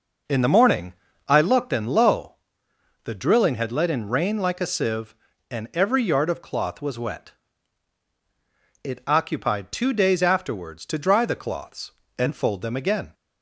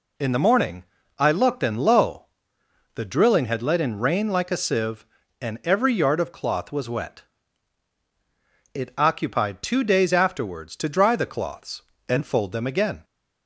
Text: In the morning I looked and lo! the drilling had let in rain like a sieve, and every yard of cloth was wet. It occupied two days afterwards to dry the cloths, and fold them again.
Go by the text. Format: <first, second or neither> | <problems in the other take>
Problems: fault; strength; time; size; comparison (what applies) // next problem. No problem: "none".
second | starts louder than the rest; noticeable; until 1.6 s; 5.5 dB // pauses between "morning" and "I"; slight; at 0.9 s; 0.34 s long; slight in the second